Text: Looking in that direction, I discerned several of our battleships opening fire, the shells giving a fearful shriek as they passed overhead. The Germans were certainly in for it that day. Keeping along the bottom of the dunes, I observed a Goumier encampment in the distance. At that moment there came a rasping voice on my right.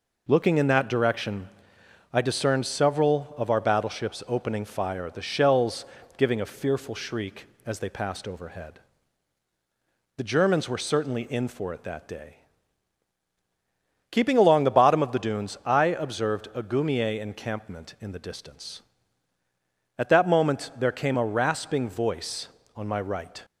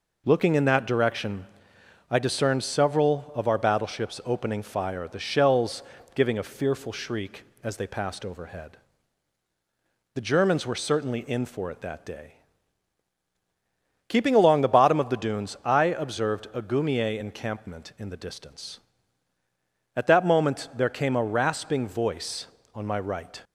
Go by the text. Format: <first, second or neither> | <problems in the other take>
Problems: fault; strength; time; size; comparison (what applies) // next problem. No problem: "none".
neither | pauses between "shells" and "giving"; slight; the same in both